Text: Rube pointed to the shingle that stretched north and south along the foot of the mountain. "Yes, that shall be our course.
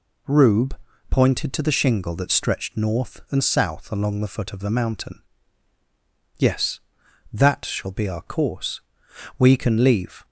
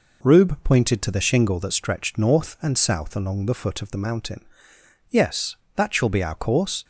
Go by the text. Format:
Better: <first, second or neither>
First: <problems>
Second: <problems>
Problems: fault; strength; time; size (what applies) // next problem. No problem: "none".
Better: second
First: pauses between "Rube" and "pointed"; slight; at 0.7 s; 0.34 s long // goes on to say "We can leave"; noticeable; from 9.3 s on; 0.88 s long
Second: none